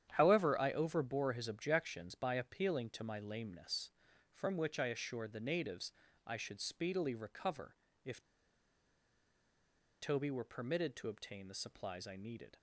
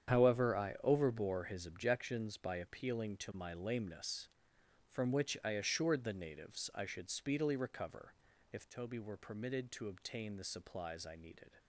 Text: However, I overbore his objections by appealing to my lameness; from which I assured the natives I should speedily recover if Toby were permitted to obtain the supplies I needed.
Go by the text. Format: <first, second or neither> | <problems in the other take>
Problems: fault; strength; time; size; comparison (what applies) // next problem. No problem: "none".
second | starts louder than the rest; strong; until 1.1 s; 9.5 dB; strong in the second // pauses between "natives" and "I"; slight; at 5.9 s; 0.34 s long // pauses between "recover" and "if"; slight; at 7.7 s; 0.28 s long; slight in the second // pauses between "if" and "Toby"; strong; at 8.2 s; 1.8 s long